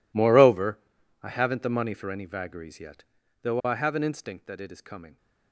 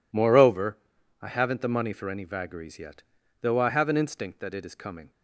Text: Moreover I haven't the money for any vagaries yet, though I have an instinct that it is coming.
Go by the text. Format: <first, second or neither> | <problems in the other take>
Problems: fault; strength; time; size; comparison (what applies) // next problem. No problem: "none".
second | gets quieter; strong; throughout; 21 dB // pauses between "Moreover" and "I"; at 0.7 s; 0.44 s long; also in the second